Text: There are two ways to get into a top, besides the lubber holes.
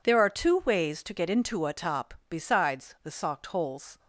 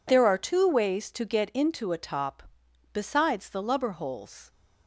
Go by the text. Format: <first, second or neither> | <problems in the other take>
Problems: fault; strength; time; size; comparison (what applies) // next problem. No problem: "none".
second | says "socked" for "lubber"; at 3.1 s